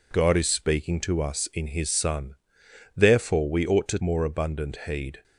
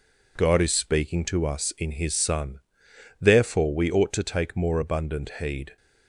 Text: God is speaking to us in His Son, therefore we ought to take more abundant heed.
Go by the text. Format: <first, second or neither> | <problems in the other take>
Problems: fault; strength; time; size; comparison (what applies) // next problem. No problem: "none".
second | skips "take"; at 3.9 s